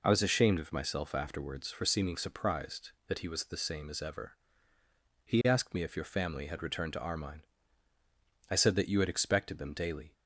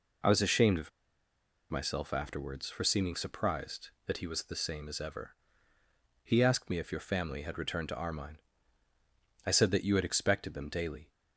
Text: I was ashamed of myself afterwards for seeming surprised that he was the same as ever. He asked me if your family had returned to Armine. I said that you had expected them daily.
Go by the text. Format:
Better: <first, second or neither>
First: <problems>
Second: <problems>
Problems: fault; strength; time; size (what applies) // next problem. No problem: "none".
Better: first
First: none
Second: pauses between "of" and "myself"; noticeable; at 0.9 s; 0.80 s long